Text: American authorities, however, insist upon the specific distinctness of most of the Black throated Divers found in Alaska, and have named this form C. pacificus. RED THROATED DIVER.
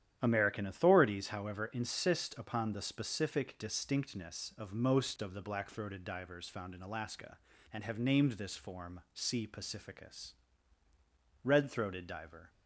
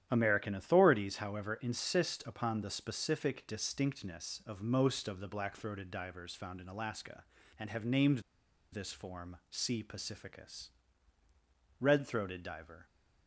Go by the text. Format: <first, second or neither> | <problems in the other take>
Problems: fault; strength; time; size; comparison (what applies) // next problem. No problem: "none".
first | starts louder than the rest; strong; until 1.1 s; 10.5 dB; strong in the first // pauses between "named" and "this"; noticeable; at 8.1 s; 0.52 s long